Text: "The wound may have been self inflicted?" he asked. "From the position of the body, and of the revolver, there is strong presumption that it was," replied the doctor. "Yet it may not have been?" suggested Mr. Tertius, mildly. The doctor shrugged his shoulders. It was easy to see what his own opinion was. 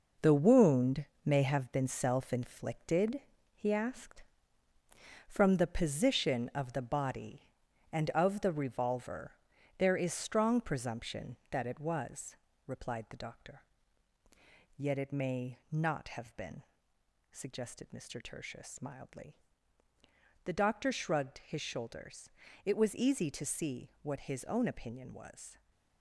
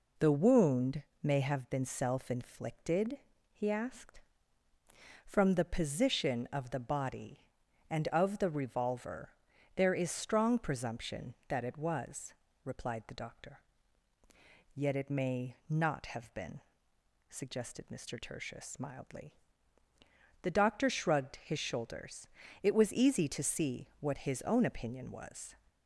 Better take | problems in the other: second | gets quieter; strong; throughout; 8 dB // pauses between "wound" and "may"; slight; at 1.0 s; 0.18 s long; slight in the second

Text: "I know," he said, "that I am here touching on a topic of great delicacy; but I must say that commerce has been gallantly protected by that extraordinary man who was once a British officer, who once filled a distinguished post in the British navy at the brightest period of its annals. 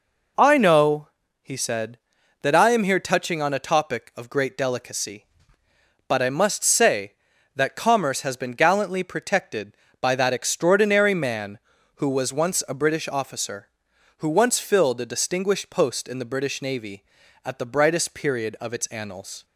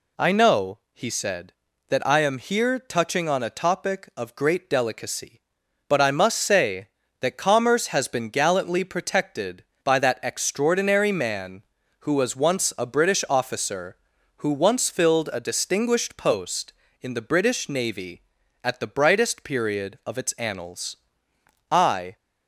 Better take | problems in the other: first | goes on to say "I"; slight; from 21.6 s on; 0.46 s long

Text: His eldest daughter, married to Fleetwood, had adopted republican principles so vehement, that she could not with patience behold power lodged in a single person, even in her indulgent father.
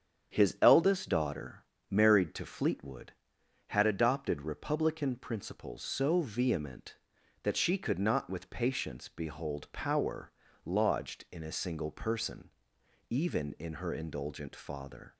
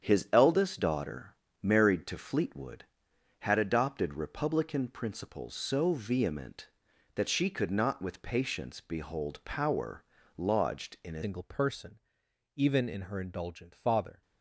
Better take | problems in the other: first | starts louder than the rest; strong; until 1.0 s; 8.5 dB; strong in the first // pauses between "power" and "lodged"; slight; at 10.0 s; 0.34 s long; slight in the first // changes voice at "single"; from 11.2 s on; 3.0 s long

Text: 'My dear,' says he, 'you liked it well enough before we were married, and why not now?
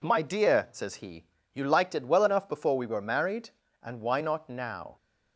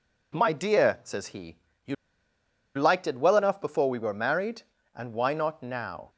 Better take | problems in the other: first | pauses between "you" and "liked"; noticeable; at 1.9 s; 0.82 s long

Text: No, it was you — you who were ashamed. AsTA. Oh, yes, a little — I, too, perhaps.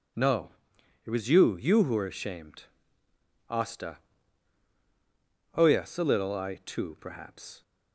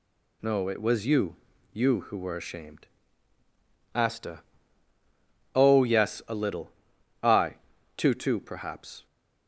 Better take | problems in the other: first | says "too" twice; at 8.1 s

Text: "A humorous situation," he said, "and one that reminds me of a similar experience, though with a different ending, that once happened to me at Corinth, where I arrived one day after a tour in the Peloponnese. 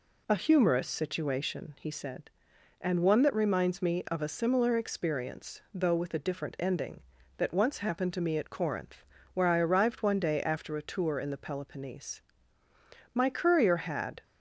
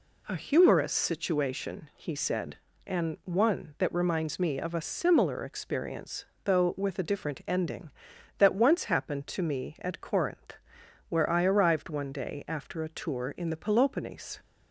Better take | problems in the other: second | goes on to say "My courier had"; noticeable; from 13.1 s on; 1.1 s long

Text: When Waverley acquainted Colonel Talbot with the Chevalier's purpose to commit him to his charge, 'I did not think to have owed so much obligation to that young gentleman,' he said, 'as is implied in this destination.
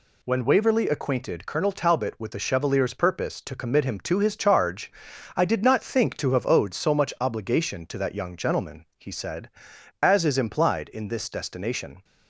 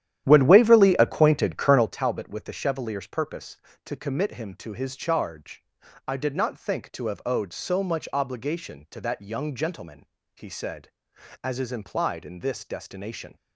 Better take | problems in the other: first | starts louder than the rest; strong; until 1.9 s; 11 dB

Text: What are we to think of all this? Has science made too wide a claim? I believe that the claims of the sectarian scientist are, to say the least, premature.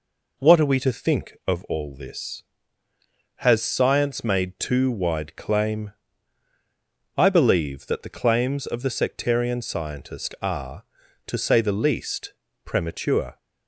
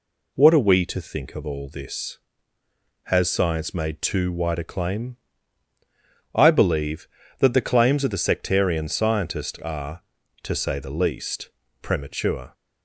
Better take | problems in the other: second | skips "a"; at 5.3 s

